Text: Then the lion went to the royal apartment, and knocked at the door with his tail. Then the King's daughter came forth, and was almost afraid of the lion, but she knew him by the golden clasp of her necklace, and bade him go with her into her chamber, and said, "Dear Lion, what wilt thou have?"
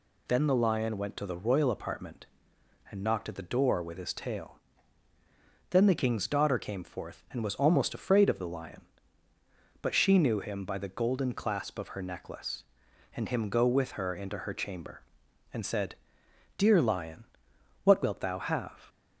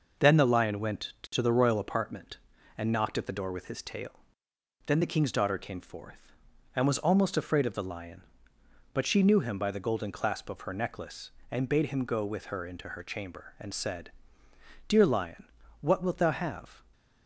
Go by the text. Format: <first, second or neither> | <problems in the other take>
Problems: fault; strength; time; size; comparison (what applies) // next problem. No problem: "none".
second | skips "bade"; at 13.2 s